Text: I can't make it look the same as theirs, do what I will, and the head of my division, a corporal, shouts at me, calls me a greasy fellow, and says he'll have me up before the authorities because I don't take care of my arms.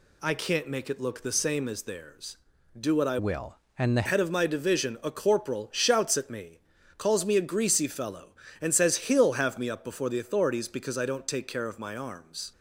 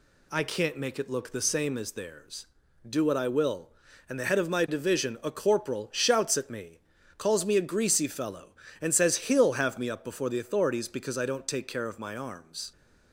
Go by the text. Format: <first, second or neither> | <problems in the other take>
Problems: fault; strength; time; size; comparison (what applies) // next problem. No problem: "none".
second | changes voice from "will" to "the"; from 3.1 to 4.0 s; 0.9 s long